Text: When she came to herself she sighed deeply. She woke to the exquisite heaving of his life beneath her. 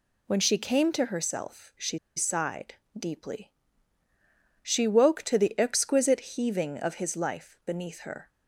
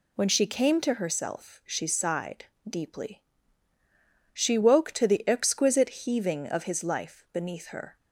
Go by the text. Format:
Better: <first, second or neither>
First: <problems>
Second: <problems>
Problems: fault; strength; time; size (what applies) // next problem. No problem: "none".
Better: second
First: pauses between "she" and "sighed"; slight; at 1.9 s; 0.18 s long // pauses between "sighed" and "deeply"; slight; at 2.7 s; 0.24 s long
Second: pauses between "sighed" and "deeply"; slight; at 2.4 s; 0.24 s long